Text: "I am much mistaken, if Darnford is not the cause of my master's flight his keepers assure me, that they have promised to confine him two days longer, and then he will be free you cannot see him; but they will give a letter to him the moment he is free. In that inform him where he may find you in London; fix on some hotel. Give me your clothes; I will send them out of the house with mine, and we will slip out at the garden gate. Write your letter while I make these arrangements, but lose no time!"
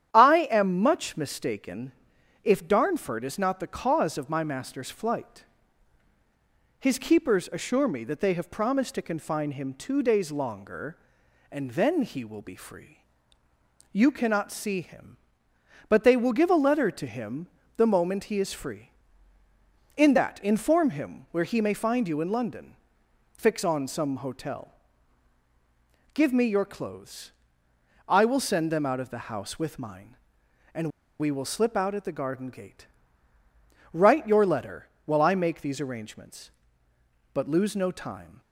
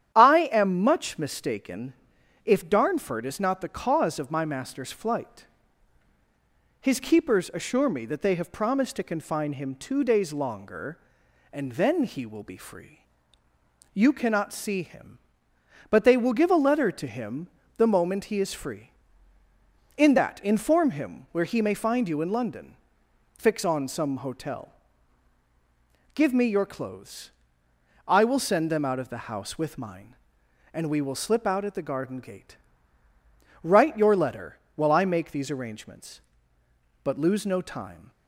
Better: second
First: starts louder than the rest; strong; until 1.1 s; 10 dB // pauses between "flight" and "his"; strong; at 5.4 s; 1.3 s long // pauses between "free" and "you"; noticeable; at 12.9 s; 0.92 s long // pauses between "him" and "the"; slight; at 17.4 s; 0.30 s long // pauses between "and" and "we"; slight; at 30.8 s; 0.30 s long // pauses between "letter" and "while"; slight; at 34.8 s; 0.18 s long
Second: starts louder than the rest; strong; until 1.1 s; 10 dB // pauses between "flight" and "his"; strong; at 5.4 s; 1.3 s long // pauses between "free" and "you"; noticeable; at 13.0 s; 0.92 s long // pauses between "him" and "the"; slight; at 17.4 s; 0.30 s long // pauses between "letter" and "while"; slight; at 34.5 s; 0.18 s long

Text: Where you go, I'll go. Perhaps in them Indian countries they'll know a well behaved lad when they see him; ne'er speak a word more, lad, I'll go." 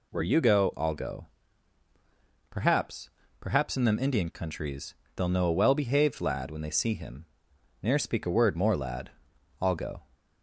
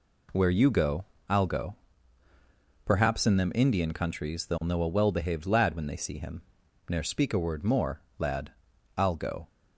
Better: second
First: says "Perhaps" twice; at 3.4 s // pauses between "countries" and "they'll"; slight; at 4.9 s; 0.20 s long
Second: none

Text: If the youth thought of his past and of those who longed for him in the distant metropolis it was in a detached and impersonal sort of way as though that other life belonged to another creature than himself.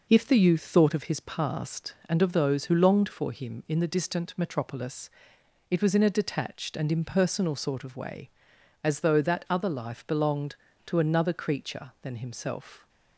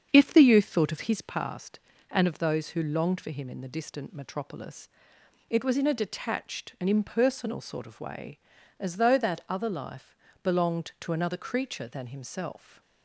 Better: first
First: pauses between "metropolis" and "it"; noticeable; at 5.1 s; 0.58 s long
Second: starts louder than the rest; strong; until 1.1 s; 7.5 dB // pauses between "metropolis" and "it"; noticeable; at 4.8 s; 0.62 s long // pauses between "life" and "belonged"; slight; at 10.1 s; 0.26 s long

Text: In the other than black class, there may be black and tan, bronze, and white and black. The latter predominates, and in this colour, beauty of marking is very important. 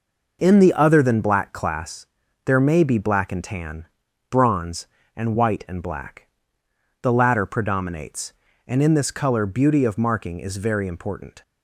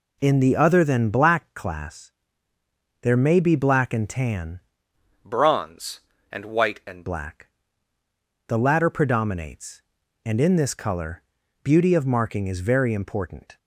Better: first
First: none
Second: changes voice from "bronze" to "and"; from 5.2 to 7.0 s; 1.8 s long

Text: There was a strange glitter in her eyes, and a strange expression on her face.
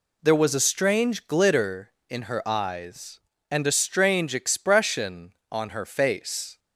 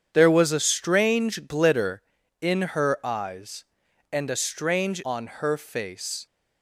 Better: first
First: none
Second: starts louder than the rest; strong; until 1.1 s; 8 dB // skips "expression"; at 5.0 s

